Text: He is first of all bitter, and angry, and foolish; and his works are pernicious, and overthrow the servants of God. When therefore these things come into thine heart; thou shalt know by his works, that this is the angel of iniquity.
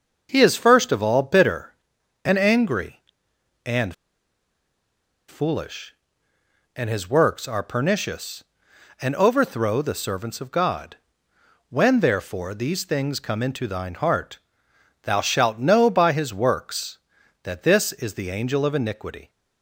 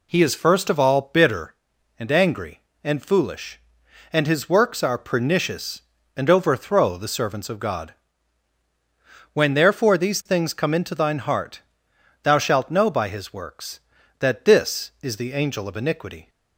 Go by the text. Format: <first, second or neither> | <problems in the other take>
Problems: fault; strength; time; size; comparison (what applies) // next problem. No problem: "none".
second | starts louder than the rest; until 1.3 s; 6.5 dB // pauses between "and" and "foolish"; strong; at 3.9 s; 1.3 s long